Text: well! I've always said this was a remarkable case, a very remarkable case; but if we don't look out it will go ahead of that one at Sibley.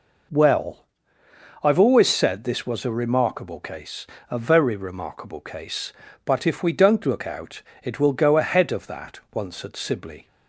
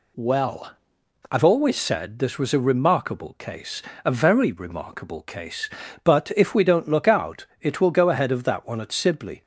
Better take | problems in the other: second | pauses between "out" and "it"; slight; at 7.6 s; 0.20 s long // says "once" for "one"; at 9.3 s

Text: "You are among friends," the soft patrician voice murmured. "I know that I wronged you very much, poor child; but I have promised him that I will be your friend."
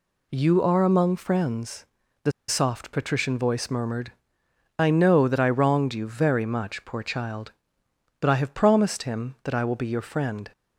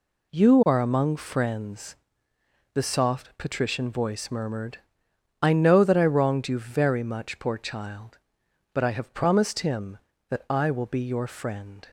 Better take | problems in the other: second | pauses between "the" and "soft"; slight; at 2.3 s; 0.18 s long

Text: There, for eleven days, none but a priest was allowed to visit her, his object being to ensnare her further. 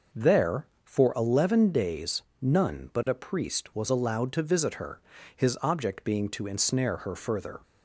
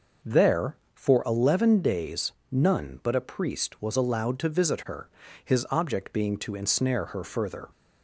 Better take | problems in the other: neither | none

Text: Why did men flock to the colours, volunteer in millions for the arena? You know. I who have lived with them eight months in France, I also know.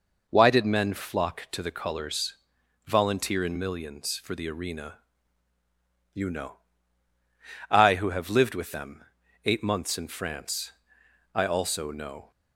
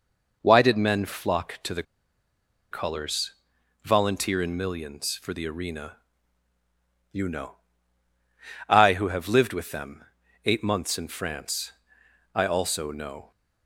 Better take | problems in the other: first | pauses between "the" and "colours"; noticeable; at 1.8 s; 0.88 s long // pauses between "them" and "eight"; at 10.0 s; 0.42 s long; also in the first

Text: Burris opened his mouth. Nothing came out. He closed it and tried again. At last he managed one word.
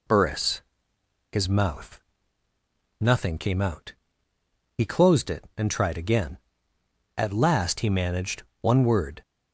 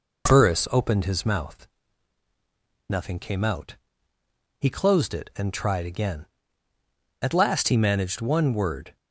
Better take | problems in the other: second | skips "opened"; at 0.9 s // pauses between "managed" and "one"; slight; at 8.4 s; 0.20 s long

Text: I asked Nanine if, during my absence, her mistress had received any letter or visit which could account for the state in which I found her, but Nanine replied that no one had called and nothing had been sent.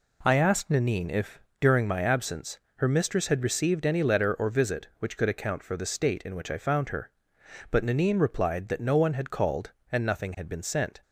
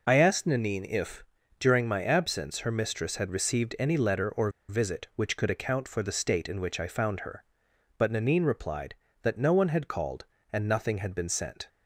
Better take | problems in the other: first | pauses between "or" and "visit"; slight; at 4.4 s; 0.19 s long

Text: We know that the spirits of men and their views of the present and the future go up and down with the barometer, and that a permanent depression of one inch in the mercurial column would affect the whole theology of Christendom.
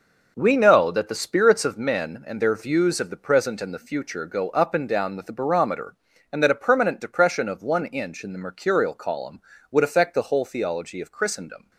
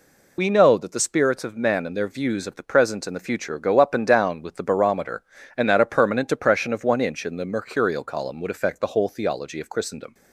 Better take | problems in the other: first | loses the start of "We"; at 0.3 s; 60 ms

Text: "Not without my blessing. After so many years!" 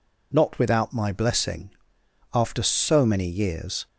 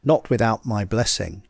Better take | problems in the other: first | stops before "After so many years"; at 1.4 s

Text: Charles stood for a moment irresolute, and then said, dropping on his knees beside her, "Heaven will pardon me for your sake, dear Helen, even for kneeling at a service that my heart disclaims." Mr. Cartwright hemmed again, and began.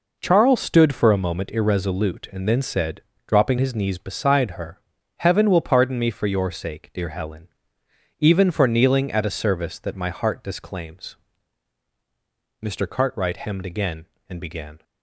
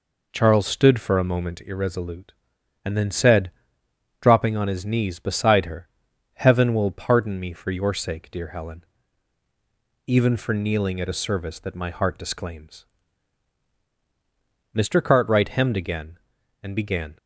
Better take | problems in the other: second | skips "on"; at 3.5 s

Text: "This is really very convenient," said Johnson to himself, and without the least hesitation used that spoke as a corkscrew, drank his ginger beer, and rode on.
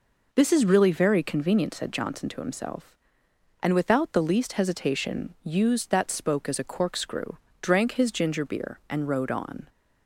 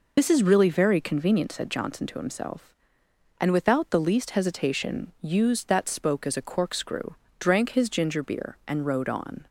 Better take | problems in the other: first | loses the start of "This"; at 0.1 s; 60 ms

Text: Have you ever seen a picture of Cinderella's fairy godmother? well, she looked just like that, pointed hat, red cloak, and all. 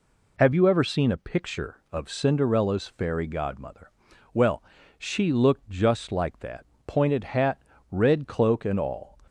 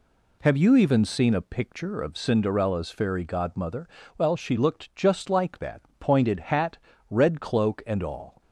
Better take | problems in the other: first | says "even" for "ever"; at 0.7 s

